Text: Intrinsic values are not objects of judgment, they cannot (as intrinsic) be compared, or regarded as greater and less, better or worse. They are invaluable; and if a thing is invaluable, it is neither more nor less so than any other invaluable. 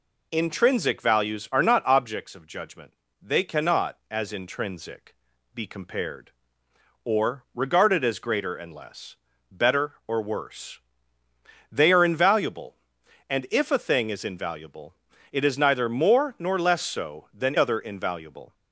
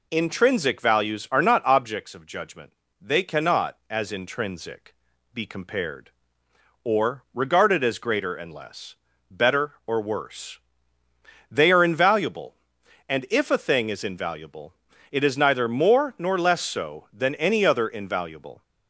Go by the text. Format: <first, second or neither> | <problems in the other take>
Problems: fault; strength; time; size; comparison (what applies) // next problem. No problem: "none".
second | skips "any"; at 17.5 s